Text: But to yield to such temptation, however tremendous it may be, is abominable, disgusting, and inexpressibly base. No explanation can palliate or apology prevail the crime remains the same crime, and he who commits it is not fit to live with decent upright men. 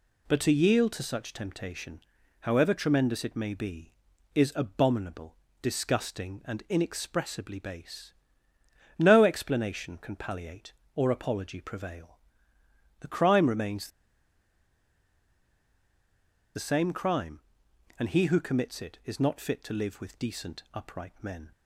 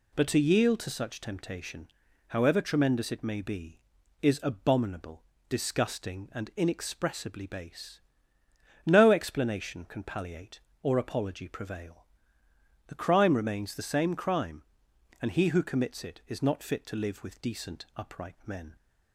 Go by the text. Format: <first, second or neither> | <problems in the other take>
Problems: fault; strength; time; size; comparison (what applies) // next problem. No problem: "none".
second | pauses between "prevail" and "the"; noticeable; at 12.1 s; 0.86 s long; noticeable in the second // pauses between "remains" and "the"; strong; at 13.8 s; 2.6 s long